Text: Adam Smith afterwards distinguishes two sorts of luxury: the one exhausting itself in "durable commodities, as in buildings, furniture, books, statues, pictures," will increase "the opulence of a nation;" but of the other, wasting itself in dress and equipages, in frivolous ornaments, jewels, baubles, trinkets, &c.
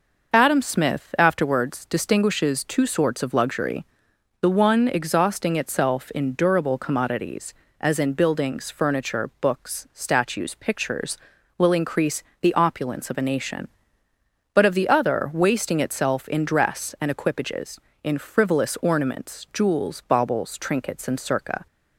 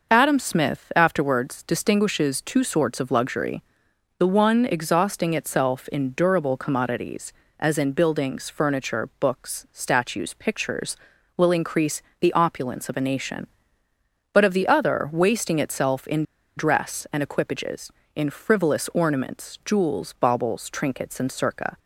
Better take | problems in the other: first | pauses between "increase" and "the"; slight; at 12.0 s; 0.18 s long; slight in the first // pauses between "in" and "dress"; slight; at 16.2 s; 0.34 s long

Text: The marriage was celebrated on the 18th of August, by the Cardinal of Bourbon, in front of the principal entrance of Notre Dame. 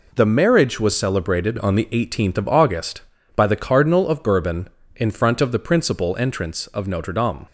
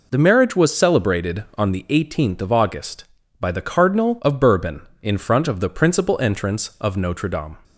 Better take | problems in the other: neither | none

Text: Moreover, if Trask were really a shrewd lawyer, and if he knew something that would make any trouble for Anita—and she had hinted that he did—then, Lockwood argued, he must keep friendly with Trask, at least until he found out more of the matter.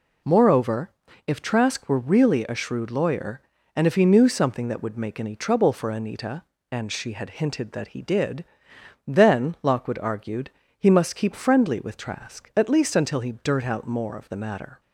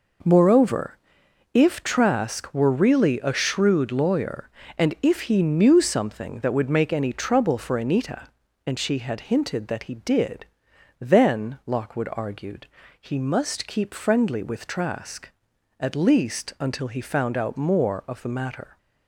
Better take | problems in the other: second | says "dirt" for "found"; at 13.3 s

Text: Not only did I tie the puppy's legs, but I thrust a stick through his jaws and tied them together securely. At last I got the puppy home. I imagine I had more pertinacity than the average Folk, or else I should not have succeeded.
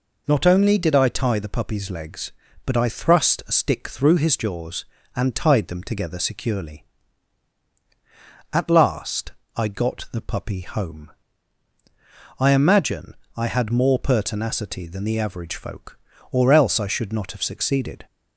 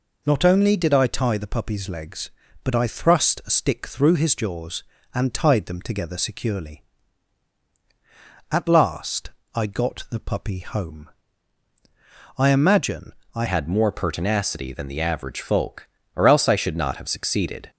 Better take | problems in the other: first | pauses between "last" and "I"; slight; at 9.3 s; 0.24 s long; slight in the first // pauses between "imagine" and "I"; slight; at 13.1 s; 0.22 s long; slight in the first // changes voice at "had"; from 13.4 s on; 4.3 s long

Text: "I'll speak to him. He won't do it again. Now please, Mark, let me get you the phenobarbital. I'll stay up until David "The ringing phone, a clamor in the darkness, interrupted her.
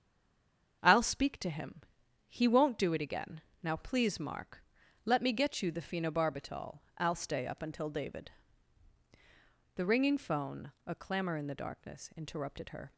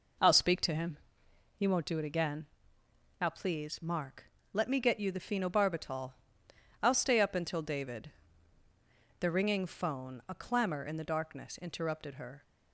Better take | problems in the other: second | stays silent before the first word; slight; until 0.8 s; 0.8 s long // starts louder than the rest; until 1.8 s; 7 dB // pauses between "David" and "The"; strong; at 8.3 s; 1.4 s long; also in the second

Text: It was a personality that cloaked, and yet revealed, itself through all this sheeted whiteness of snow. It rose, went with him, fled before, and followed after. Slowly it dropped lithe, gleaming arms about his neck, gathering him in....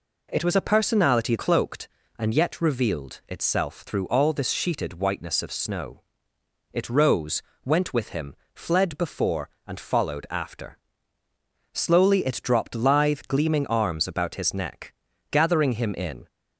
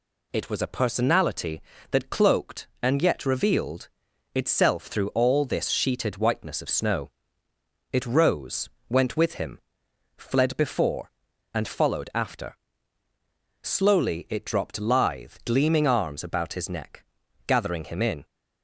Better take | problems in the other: second | skips "that"; at 1.3 s

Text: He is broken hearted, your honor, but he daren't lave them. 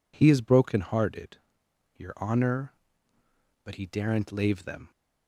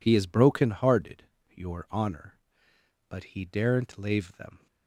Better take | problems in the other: neither | none

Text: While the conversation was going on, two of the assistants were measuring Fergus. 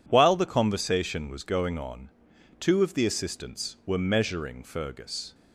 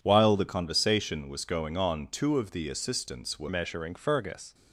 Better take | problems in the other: first | changes voice at "measuring"; from 3.4 s on; 1.1 s long

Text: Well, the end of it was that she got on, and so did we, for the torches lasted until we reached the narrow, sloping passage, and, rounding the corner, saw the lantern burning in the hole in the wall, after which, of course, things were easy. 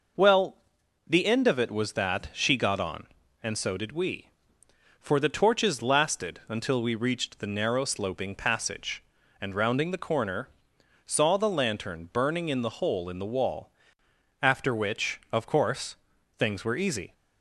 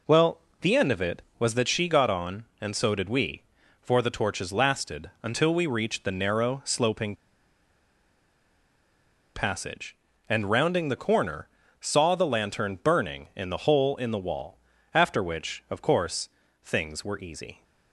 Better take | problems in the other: first | pauses between "sloping" and "passage"; strong; at 7.1 s; 2.2 s long

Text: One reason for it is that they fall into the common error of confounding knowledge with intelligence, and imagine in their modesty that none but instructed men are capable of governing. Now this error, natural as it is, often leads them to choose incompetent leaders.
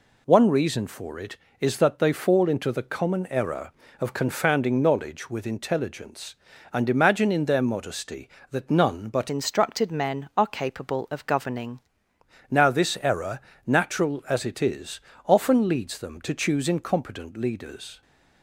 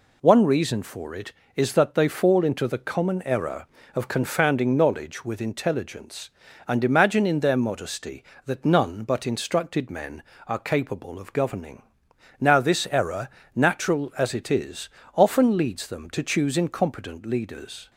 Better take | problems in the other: second | changes voice from "instructed" to "governing"; from 9.2 to 11.7 s; 2.5 s long

